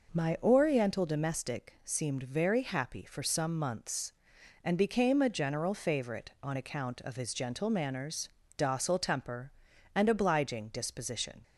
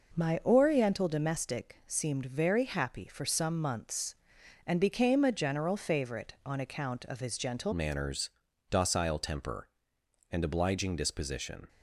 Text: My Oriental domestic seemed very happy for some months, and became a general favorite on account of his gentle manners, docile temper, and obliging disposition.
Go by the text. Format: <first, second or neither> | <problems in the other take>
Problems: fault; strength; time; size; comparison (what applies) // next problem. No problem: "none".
first | changes voice at "manners"; from 7.7 s on; 3.9 s long